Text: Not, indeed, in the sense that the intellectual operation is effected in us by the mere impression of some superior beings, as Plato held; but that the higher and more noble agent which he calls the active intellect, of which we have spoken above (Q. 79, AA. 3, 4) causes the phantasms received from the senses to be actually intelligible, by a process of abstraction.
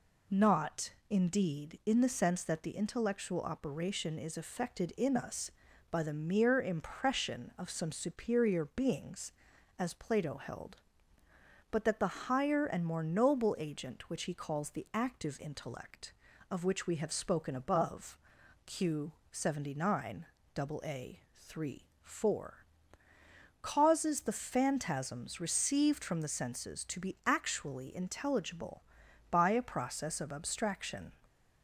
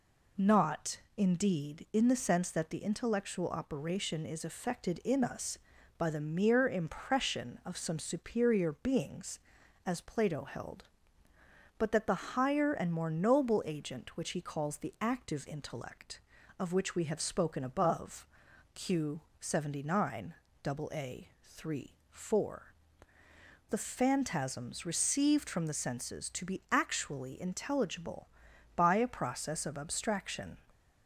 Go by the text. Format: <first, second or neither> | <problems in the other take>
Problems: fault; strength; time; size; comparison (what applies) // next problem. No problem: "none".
first | skips "causes"; at 23.2 s